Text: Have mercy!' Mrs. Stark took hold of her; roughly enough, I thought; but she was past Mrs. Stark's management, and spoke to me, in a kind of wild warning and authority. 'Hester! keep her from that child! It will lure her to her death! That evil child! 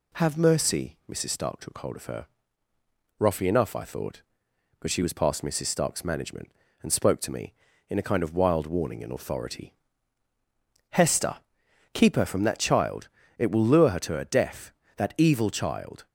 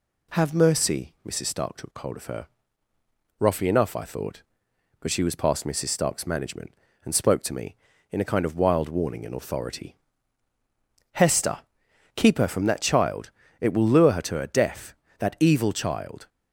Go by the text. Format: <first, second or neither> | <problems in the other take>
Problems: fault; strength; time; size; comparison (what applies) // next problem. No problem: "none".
neither | none